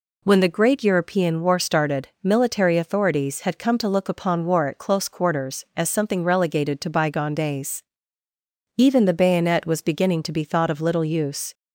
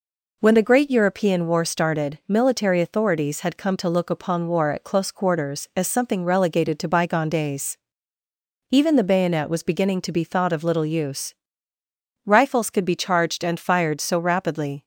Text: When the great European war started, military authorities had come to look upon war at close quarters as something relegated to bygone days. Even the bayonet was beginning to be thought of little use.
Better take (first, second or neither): first